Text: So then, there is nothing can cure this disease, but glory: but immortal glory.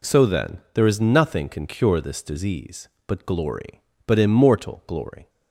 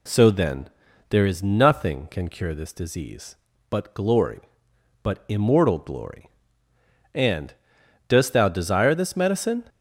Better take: first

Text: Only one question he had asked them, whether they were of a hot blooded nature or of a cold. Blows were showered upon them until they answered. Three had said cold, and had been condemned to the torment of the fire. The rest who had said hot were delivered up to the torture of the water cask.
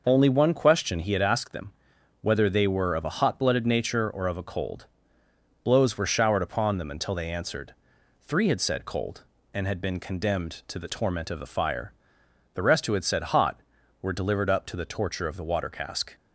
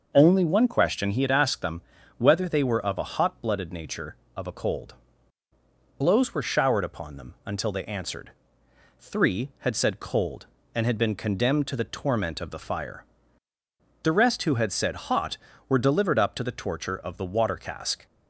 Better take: first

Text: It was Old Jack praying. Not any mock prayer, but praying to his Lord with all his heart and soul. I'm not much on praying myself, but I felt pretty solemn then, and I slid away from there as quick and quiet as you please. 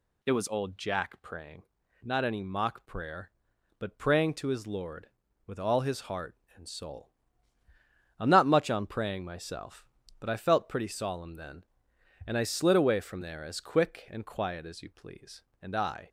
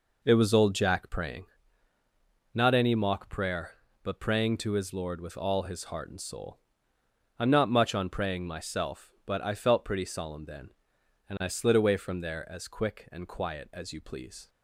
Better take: second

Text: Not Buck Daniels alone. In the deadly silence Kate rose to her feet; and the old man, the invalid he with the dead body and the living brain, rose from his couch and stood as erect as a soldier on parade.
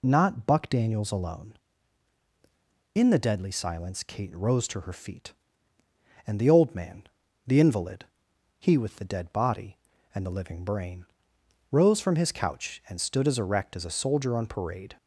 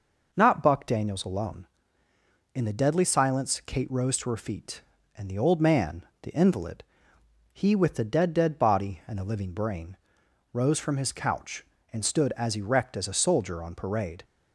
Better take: first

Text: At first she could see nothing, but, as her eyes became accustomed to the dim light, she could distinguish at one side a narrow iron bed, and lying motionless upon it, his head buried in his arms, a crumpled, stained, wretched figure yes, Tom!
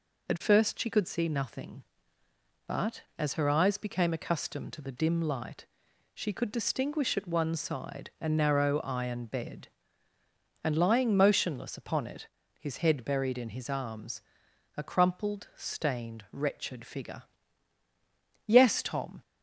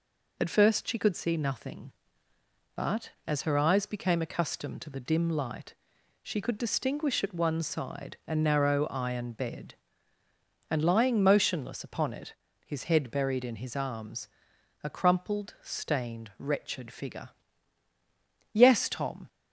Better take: neither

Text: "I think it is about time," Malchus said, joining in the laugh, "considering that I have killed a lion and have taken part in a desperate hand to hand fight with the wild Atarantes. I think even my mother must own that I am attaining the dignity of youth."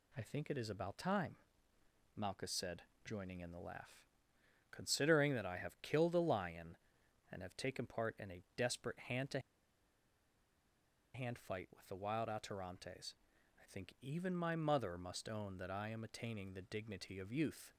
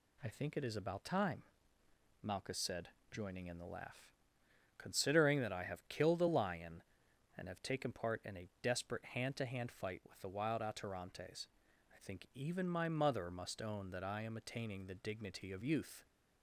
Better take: second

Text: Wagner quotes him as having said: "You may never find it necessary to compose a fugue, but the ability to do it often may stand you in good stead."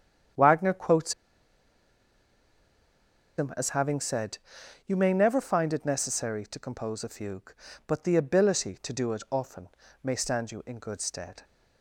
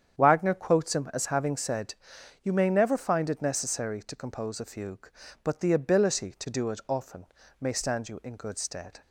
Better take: second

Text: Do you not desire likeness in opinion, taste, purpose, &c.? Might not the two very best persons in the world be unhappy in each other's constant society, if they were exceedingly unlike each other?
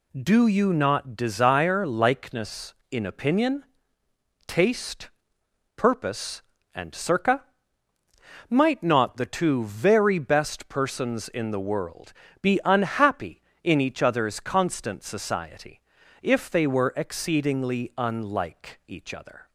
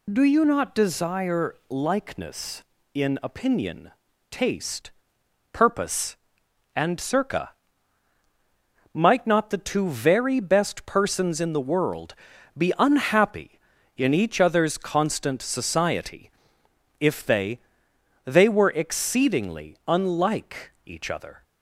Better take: first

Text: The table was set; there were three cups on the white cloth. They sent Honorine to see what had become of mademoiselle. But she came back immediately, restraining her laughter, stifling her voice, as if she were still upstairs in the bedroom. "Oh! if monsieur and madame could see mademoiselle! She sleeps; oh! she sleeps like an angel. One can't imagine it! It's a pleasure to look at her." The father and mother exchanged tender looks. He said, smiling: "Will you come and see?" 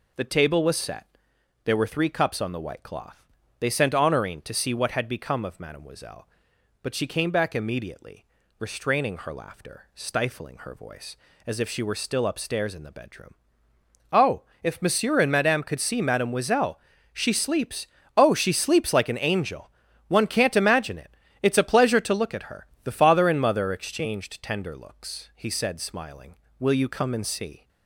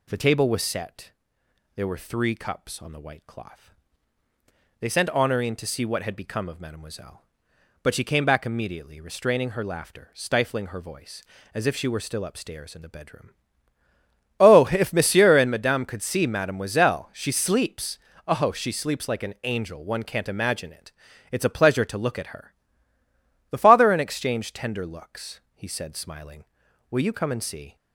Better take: first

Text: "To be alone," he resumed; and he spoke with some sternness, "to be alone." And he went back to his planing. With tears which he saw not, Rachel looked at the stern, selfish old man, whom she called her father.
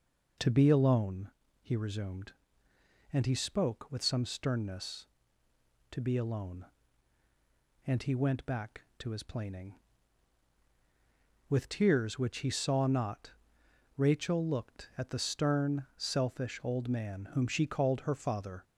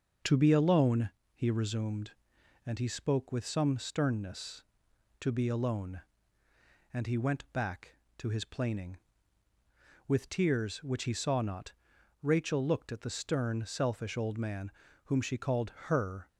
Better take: first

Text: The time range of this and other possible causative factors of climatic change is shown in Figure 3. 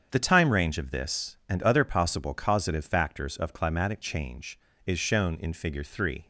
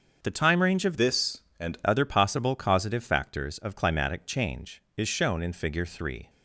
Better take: first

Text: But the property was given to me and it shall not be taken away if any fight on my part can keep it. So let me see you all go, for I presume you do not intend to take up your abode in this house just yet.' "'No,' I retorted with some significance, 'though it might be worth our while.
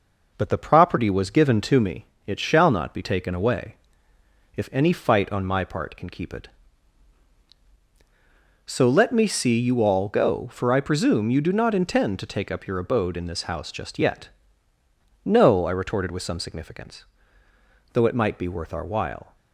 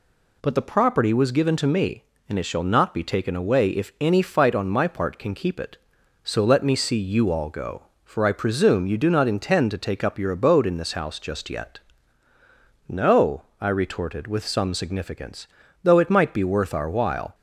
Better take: second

